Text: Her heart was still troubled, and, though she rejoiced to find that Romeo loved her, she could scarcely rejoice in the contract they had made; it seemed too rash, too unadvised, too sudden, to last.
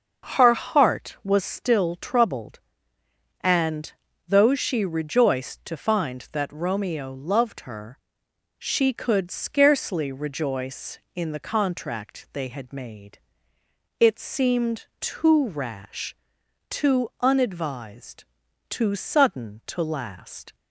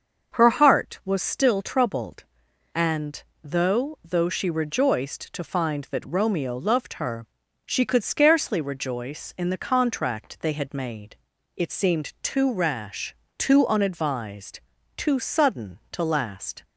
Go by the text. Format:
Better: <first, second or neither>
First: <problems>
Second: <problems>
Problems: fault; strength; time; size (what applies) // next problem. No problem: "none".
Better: first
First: starts louder than the rest; noticeable; until 1.3 s; 6 dB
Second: starts louder than the rest; until 1.4 s; 6.5 dB // says "though" twice; at 4.0 s